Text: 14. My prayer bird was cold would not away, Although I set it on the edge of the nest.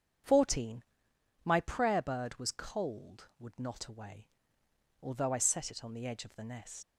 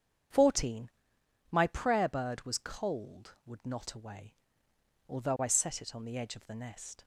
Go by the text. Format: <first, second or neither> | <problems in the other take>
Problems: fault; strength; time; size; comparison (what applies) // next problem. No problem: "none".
second | starts louder than the rest; strong; until 1.8 s; 8 dB; strong in the second // leaves "nest" unfinished; at 6.8 s; 100 ms